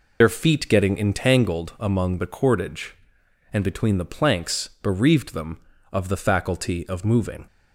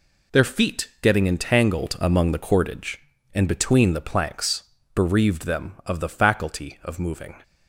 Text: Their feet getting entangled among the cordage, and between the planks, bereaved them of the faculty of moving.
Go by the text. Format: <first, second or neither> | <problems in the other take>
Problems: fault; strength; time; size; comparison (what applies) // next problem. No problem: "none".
second | loses the start of "Their"; at 0.2 s; 60 ms